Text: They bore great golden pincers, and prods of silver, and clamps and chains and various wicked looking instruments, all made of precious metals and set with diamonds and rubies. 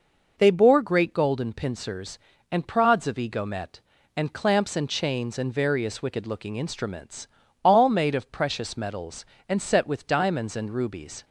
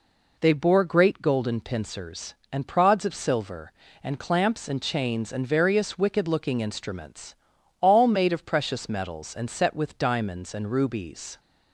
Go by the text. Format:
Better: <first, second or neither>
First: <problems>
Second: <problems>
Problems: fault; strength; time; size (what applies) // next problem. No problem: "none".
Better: second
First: says "egomet" for "silver"; at 3.1 s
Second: none